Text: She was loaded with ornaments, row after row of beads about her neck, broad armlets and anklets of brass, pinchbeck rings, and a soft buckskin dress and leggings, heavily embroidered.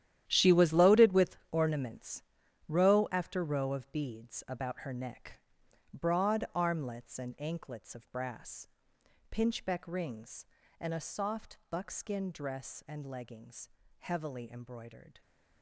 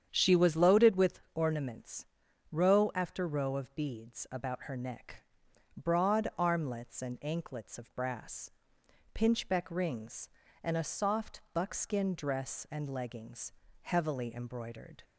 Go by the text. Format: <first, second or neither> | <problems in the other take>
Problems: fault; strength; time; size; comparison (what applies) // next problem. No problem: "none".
second | gets quieter; strong; throughout; 13.5 dB // starts louder than the rest; strong; until 1.2 s; 11.5 dB; strong in the second